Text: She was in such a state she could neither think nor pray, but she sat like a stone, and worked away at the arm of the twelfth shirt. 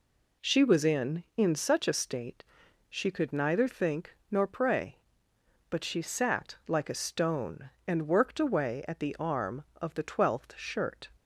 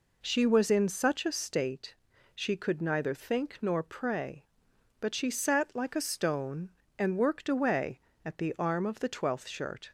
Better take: second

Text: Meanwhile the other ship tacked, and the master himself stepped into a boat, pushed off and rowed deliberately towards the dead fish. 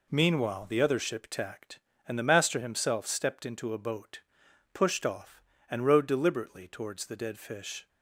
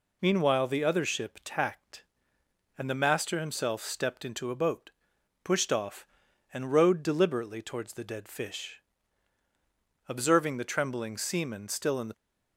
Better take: first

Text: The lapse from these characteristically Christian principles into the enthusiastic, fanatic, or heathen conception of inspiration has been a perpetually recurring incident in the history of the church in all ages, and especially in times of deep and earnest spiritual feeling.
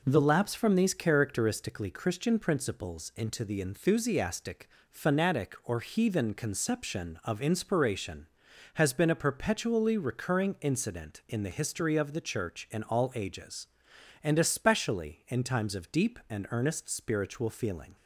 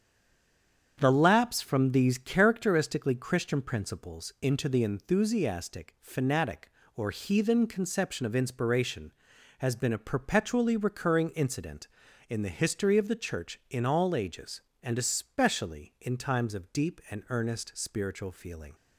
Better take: first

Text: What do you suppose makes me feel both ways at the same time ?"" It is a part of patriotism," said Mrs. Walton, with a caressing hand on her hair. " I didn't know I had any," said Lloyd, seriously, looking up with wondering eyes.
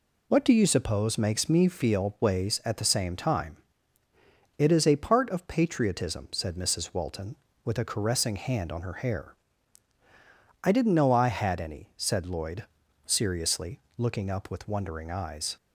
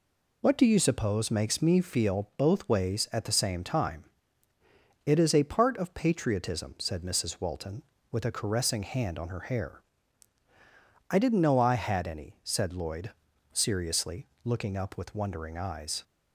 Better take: second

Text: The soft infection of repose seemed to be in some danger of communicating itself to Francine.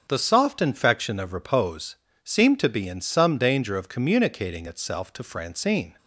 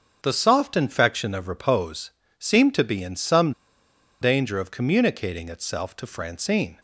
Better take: first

